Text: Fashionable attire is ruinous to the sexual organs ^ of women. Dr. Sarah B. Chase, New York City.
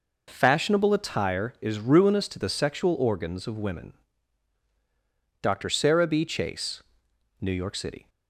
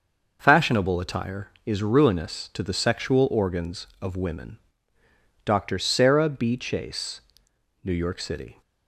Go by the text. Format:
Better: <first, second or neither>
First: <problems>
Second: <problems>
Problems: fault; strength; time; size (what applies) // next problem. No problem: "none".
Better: neither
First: none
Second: none